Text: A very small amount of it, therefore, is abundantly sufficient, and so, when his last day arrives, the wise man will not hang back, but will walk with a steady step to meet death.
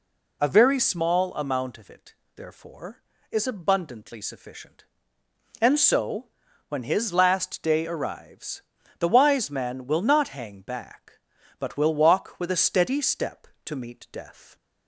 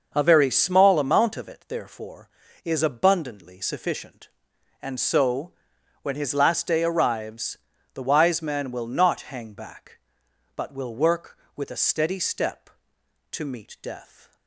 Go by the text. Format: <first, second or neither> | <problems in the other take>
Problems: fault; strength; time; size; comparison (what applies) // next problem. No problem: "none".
first | says "work" for "walk"; at 10.9 s